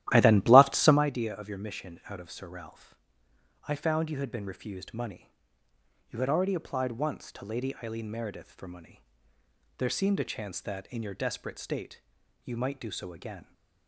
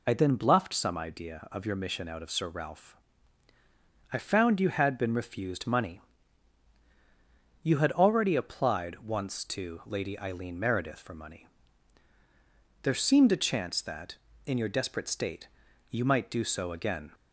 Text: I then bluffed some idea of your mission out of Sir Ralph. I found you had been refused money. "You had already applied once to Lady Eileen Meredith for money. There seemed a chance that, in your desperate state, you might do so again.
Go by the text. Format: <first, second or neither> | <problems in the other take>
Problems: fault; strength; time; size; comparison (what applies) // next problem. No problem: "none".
second | starts louder than the rest; strong; until 1.1 s; 14 dB